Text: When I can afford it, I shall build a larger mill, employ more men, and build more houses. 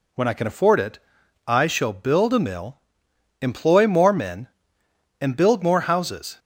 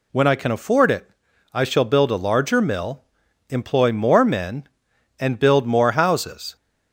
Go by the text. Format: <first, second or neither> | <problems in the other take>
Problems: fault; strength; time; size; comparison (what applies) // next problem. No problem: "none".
second | skips "larger"; at 2.3 s